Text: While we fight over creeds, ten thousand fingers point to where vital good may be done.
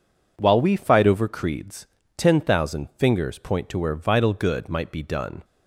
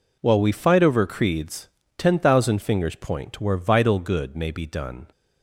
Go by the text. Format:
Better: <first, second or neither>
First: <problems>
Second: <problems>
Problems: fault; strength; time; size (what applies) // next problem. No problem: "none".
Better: second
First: says "might" for "may"; at 4.6 s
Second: none